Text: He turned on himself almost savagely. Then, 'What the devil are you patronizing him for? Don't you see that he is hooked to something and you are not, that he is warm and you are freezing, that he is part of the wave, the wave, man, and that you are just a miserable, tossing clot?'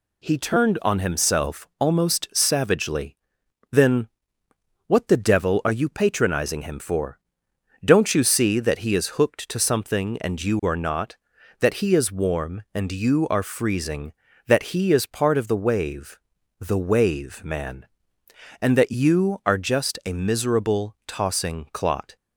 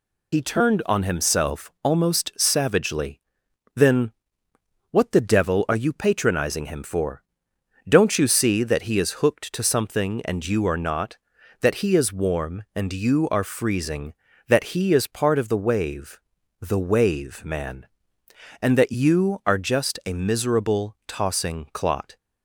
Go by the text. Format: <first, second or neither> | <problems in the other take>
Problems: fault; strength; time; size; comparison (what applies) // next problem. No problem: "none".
first | loses the start of "He"; at 0.3 s; 60 ms